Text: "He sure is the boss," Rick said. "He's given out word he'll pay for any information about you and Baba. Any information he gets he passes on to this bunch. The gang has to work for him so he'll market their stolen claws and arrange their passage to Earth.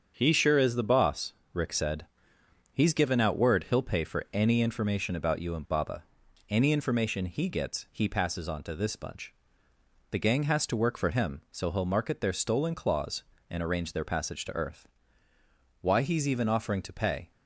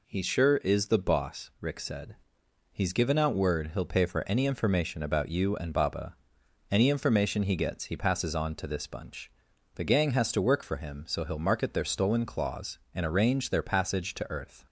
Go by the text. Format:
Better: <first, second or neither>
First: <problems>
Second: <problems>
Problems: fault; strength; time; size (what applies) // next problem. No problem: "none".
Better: second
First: starts louder than the rest; strong; until 1.1 s; 7.5 dB // goes on to say "Why he's even offering to pay"; from 15.8 s on; 1.4 s long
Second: none